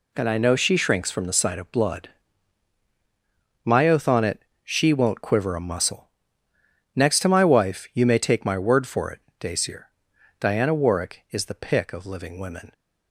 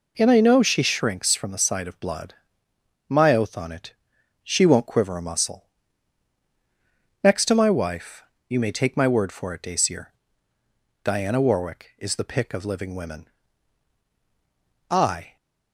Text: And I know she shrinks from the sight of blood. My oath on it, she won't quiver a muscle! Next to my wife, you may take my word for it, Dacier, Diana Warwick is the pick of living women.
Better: first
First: none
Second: goes on to say "I"; slight; from 14.8 s on; 0.46 s long

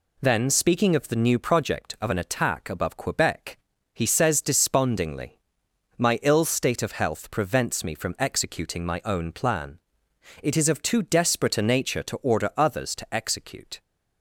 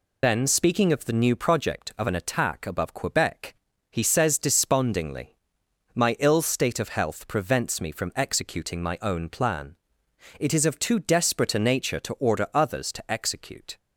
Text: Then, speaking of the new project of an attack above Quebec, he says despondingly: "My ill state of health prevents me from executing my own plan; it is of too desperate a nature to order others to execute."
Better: first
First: none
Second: loses the start of "Then"; at 0.2 s; 70 ms

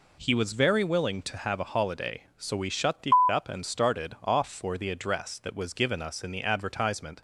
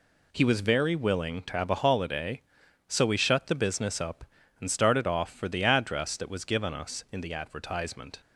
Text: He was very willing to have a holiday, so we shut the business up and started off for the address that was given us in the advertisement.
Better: second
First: skips "business"; at 3.2 s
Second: none

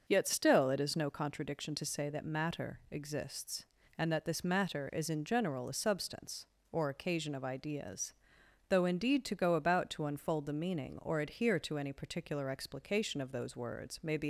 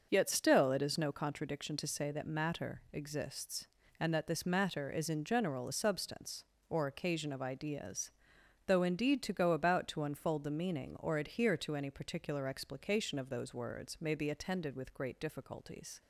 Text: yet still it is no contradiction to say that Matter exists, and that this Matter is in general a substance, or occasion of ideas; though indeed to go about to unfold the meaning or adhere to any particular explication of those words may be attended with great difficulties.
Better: second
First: starts louder than the rest; until 1.0 s; 6.5 dB // stops before "attended with great difficulties"; at 14.2 s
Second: starts louder than the rest; until 1.1 s; 6.5 dB

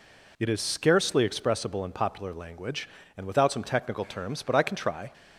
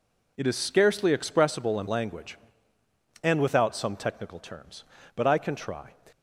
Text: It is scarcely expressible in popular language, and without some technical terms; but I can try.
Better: first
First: none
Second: skips "popular"; at 1.8 s

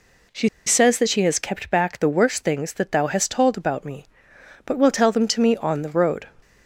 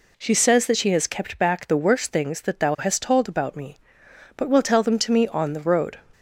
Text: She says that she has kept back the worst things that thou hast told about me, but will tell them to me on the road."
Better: second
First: pauses between "She" and "says"; slight; at 0.4 s; 0.17 s long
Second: none

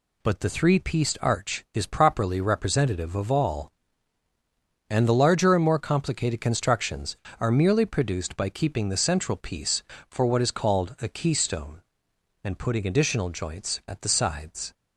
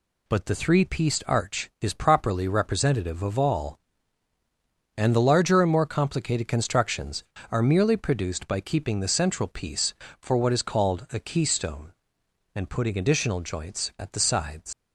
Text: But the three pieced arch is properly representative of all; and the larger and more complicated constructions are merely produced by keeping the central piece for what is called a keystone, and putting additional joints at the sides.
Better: first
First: none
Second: leaves "sides" unfinished; at 14.7 s; 110 ms

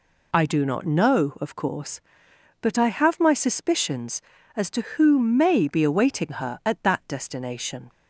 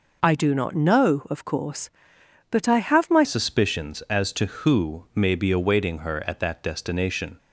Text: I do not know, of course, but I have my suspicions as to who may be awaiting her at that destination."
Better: first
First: none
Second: changes voice at "suspicions"; from 3.2 s on; 4.1 s long

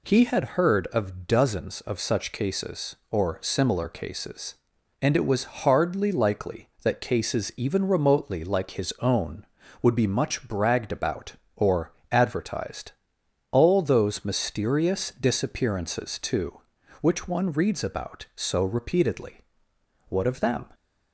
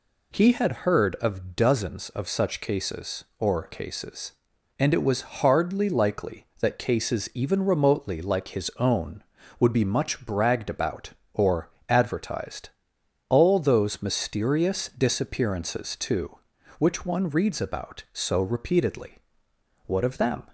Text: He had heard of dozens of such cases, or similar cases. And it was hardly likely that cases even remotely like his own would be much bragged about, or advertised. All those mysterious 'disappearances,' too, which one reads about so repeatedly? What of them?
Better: first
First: pauses between "or" and "advertised"; slight; at 11.9 s; 0.18 s long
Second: skips "similar"; at 3.6 s // pauses between "or" and "advertised"; slight; at 11.7 s; 0.18 s long

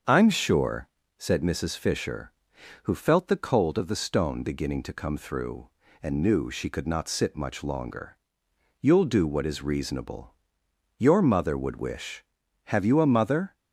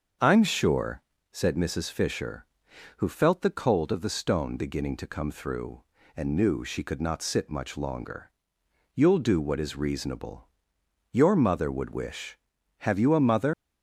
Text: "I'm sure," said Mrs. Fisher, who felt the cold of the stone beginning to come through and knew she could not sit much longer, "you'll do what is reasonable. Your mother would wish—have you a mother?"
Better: first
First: starts louder than the rest; until 1.3 s; 6.5 dB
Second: starts louder than the rest; until 1.5 s; 6.5 dB // leaves "mother" unfinished; at 13.5 s; 150 ms

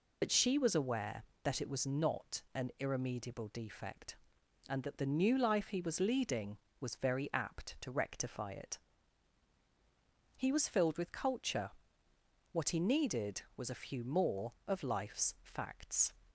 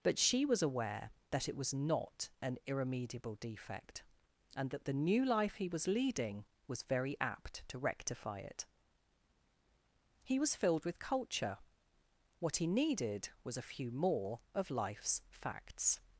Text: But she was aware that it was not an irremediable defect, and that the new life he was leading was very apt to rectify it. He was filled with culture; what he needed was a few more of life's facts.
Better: second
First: loses the start of "But"; at 0.2 s; 55 ms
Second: none

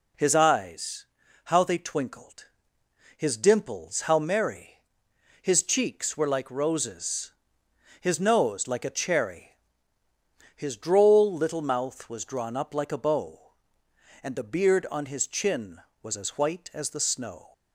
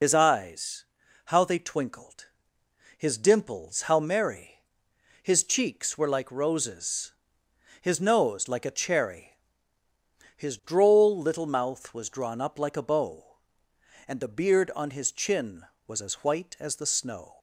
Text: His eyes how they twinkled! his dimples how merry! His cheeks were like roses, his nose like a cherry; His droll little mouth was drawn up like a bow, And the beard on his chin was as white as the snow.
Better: first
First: pauses between "eyes" and "how"; at 1.0 s; 0.40 s long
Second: loses the start of "His"; at 0.0 s; 70 ms // pauses between "eyes" and "how"; at 0.8 s; 0.42 s long

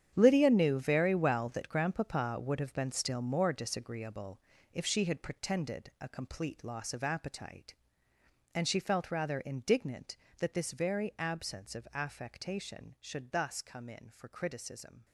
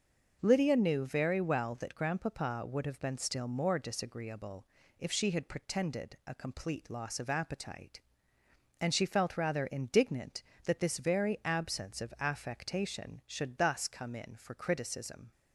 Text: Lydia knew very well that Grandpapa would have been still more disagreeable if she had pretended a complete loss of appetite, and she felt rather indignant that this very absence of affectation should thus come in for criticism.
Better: second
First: gets quieter; strong; throughout; 13 dB // starts louder than the rest; strong; until 1.1 s; 9 dB // pauses between "disagreeable" and "if"; slight; at 4.3 s; 0.32 s long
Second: starts louder than the rest; noticeable; until 1.4 s; 6 dB // pauses between "disagreeable" and "if"; slight; at 4.6 s; 0.32 s long

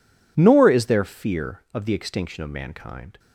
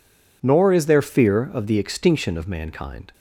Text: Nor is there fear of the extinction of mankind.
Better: neither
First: none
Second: none

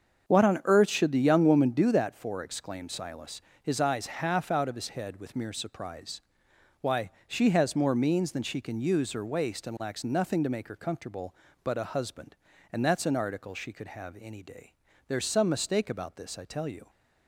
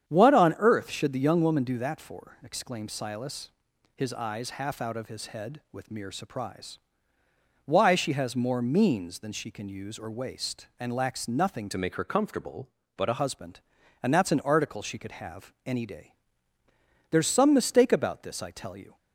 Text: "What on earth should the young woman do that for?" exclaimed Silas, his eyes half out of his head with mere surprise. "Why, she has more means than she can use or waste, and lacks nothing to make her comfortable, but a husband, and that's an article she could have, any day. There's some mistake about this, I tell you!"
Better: first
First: starts louder than the rest; strong; until 1.3 s; 7.5 dB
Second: starts louder than the rest; strong; until 1.1 s; 9 dB // changes voice from "to" to "a"; from 11.7 to 13.1 s; 1.4 s long

